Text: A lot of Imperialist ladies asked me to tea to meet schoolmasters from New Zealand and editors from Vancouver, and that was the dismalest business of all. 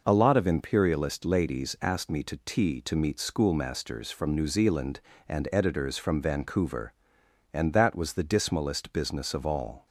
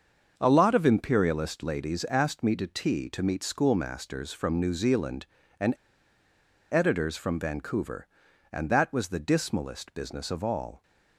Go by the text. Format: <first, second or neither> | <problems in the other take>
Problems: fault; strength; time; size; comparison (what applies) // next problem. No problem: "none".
first | starts louder than the rest; until 1.3 s; 6.5 dB // pauses between "and" and "editors"; at 5.7 s; 0.98 s long